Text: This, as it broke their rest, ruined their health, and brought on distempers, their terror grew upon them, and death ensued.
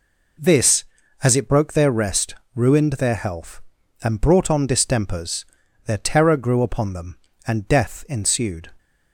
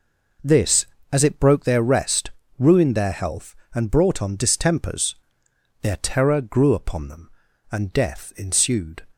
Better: neither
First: none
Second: none

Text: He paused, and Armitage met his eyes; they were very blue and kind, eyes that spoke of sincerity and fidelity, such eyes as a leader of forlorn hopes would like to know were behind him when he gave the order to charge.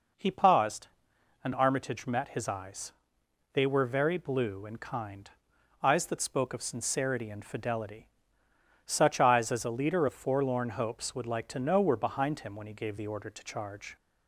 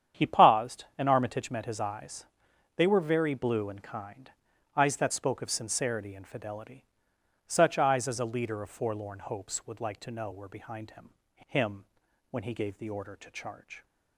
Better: first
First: none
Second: starts louder than the rest; strong; until 1.2 s; 9 dB // says "him" twice; at 11.4 s

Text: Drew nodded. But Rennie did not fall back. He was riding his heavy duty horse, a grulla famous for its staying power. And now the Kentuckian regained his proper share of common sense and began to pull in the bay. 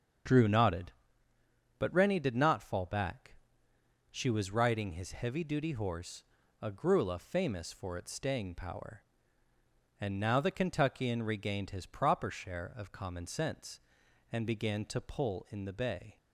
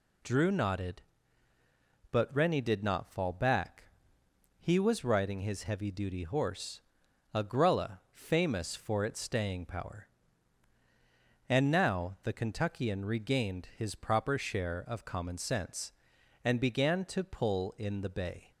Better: second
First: starts louder than the rest; until 2.1 s; 7 dB // says "She" for "He"; at 4.1 s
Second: none

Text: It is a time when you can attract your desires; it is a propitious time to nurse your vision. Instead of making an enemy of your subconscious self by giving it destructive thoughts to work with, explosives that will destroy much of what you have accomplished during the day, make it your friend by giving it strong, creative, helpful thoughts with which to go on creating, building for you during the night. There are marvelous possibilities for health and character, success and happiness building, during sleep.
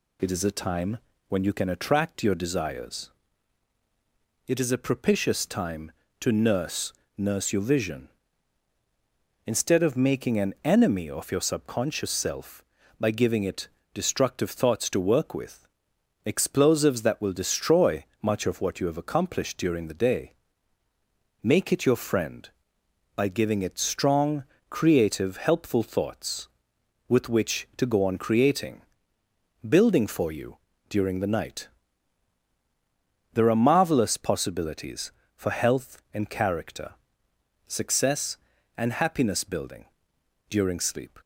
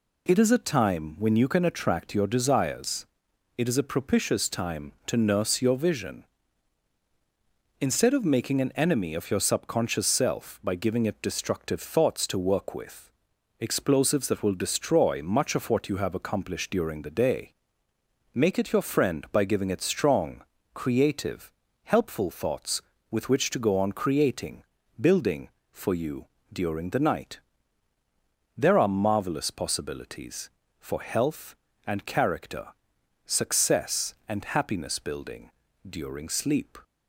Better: second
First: pauses between "time" and "when"; slight; at 0.9 s; 0.30 s long // says "nurse" twice; at 7.1 s // pauses between "it" and "destructive"; slight; at 13.6 s; 0.26 s long // pauses between "destroy" and "much"; slight; at 18.0 s; 0.16 s long // pauses between "you" and "during"; slight; at 30.5 s; 0.32 s long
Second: pauses between "you" and "during"; slight; at 26.2 s; 0.26 s long

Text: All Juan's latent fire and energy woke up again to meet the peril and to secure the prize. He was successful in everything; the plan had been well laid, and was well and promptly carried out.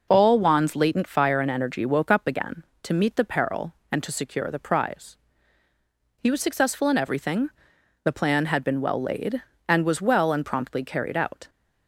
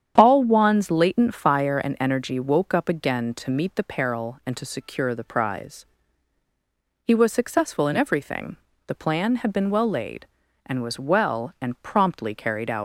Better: first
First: none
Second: starts louder than the rest; strong; until 1.1 s; 8.5 dB // leaves "out" unfinished; at 12.7 s; 80 ms

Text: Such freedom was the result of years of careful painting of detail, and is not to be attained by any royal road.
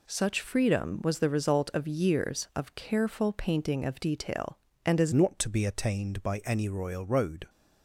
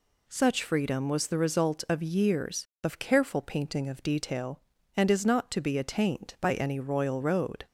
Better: second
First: changes voice at "not"; from 5.1 s on; 2.3 s long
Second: none

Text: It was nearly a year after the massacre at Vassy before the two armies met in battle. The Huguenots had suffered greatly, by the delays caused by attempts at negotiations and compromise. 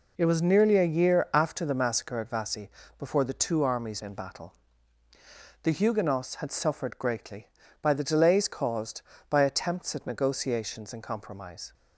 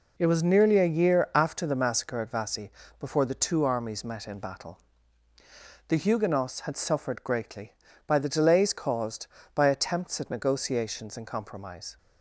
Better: second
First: pauses between "Vassy" and "before"; slight; at 2.6 s; 0.28 s long // skips "met"; at 4.0 s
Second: pauses between "Vassy" and "before"; slight; at 2.7 s; 0.28 s long

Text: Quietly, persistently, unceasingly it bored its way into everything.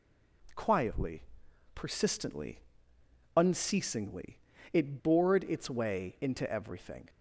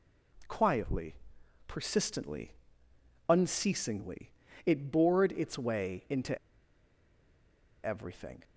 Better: first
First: pauses between "unceasingly" and "it"; slight; at 4.3 s; 0.34 s long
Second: pauses between "unceasingly" and "it"; slight; at 4.3 s; 0.34 s long // pauses between "into" and "everything"; strong; at 6.3 s; 1.4 s long

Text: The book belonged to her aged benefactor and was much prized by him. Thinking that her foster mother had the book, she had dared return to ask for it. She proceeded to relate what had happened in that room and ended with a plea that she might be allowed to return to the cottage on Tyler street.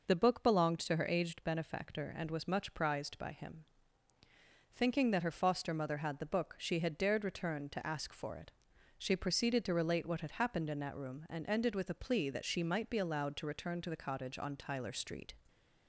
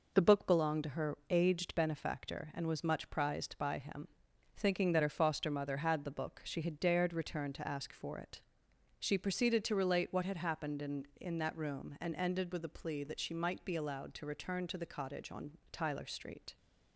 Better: first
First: none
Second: says "in" twice; at 11.2 s // pauses between "on" and "Tyler"; slight; at 15.5 s; 0.18 s long

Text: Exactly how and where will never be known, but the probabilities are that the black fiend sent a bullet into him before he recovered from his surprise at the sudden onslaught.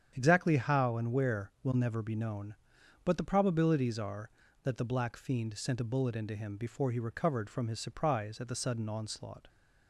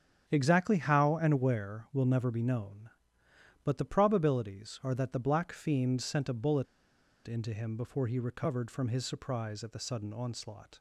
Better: first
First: starts louder than the rest; strong; until 1.1 s; 8.5 dB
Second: starts louder than the rest; strong; until 1.2 s; 8.5 dB // pauses between "bullet" and "into"; noticeable; at 6.6 s; 0.60 s long

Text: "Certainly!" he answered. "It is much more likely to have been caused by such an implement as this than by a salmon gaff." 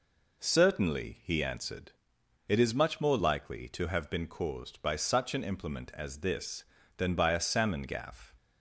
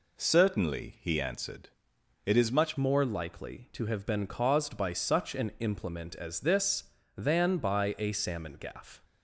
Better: first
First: none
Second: changes voice at "more"; from 2.7 s on; 6.3 s long

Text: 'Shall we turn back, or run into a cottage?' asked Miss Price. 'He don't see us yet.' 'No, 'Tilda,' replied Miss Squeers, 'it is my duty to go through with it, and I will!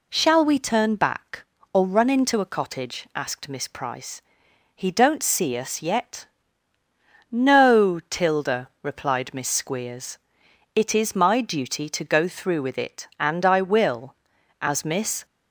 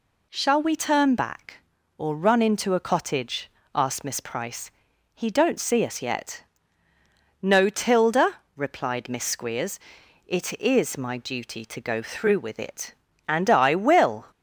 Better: second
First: goes on to say "As Miss"; noticeable; from 14.6 s on; 0.62 s long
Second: none

